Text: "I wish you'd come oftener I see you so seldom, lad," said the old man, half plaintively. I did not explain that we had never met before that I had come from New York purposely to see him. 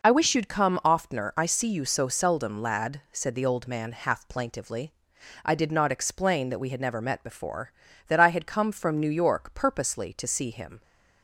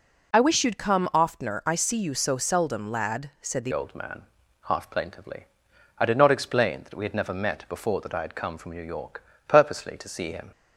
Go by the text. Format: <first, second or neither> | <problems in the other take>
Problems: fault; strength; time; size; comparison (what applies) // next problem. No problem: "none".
first | changes voice at "old"; from 3.7 s on; 6.8 s long // pauses between "York" and "purposely"; slight; at 9.2 s; 0.22 s long